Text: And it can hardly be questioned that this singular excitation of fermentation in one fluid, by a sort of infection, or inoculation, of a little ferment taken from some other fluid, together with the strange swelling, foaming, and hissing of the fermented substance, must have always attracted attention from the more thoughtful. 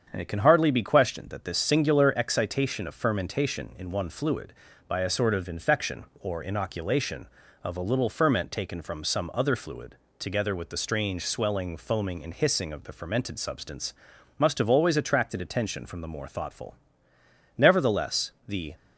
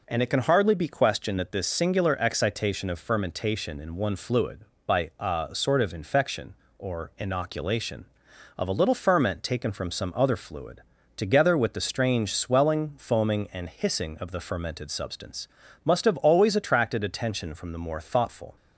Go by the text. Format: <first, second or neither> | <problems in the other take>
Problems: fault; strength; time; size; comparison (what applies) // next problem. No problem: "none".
second | starts louder than the rest; strong; until 1.1 s; 7.5 dB // goes on to say "Nevertheless the"; noticeable; from 17.5 s on; 1.1 s long